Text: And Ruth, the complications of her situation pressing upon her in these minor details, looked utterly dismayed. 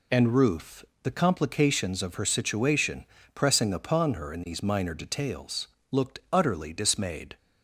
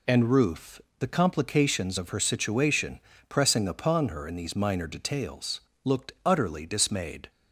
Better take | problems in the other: neither | pauses between "situation" and "pressing"; slight; the same in both

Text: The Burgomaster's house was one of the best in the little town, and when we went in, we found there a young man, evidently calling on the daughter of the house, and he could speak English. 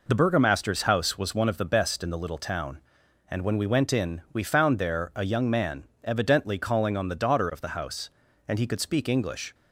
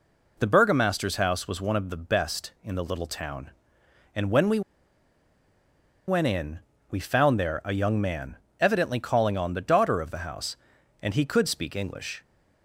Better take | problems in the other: first | pauses between "we" and "went"; strong; at 4.6 s; 1.4 s long

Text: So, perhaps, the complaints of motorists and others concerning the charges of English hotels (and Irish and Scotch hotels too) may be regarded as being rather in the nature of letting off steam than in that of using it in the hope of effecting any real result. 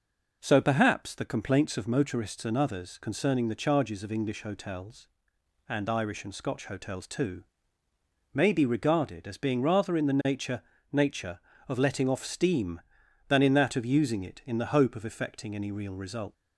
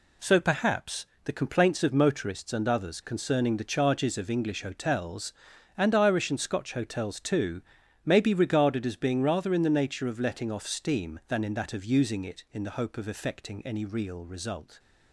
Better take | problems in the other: second | says "nature" twice; at 10.9 s

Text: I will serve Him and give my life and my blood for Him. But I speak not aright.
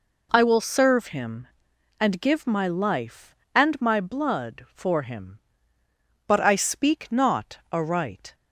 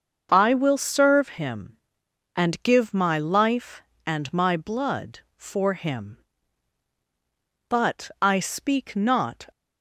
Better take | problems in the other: first | starts louder than the rest; until 1.3 s; 7 dB // stops before "aright"; at 9.5 s

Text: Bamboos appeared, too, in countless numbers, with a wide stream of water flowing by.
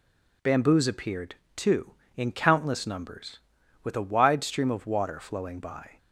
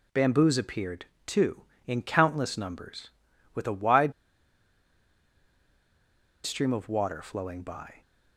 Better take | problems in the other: first | pauses between "wide" and "stream"; strong; at 4.1 s; 2.3 s long

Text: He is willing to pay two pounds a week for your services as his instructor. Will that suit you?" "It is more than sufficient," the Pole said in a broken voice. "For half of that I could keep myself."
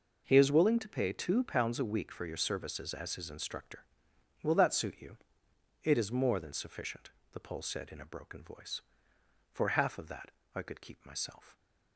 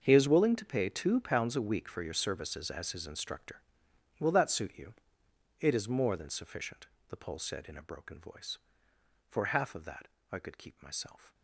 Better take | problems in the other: first | gets quieter; strong; throughout; 16 dB // pauses between "that" and "I"; slight; at 10.0 s; 0.24 s long; slight in the first

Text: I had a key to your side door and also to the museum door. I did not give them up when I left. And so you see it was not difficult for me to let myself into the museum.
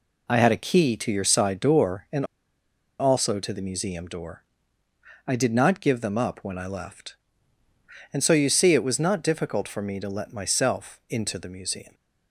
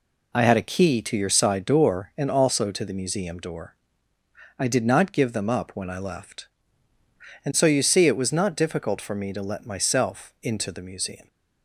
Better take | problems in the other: second | pauses between "and" and "also"; noticeable; at 2.2 s; 0.74 s long

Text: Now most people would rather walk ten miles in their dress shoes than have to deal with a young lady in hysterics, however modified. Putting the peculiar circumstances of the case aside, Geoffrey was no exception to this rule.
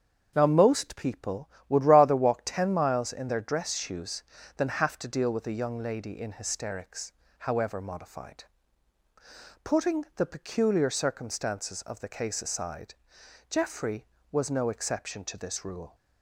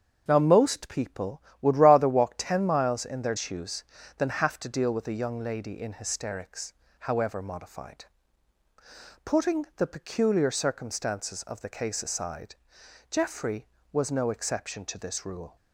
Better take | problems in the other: first | starts louder than the rest; strong; until 1.2 s; 7 dB; strong in the first // skips "dress"; at 3.3 s

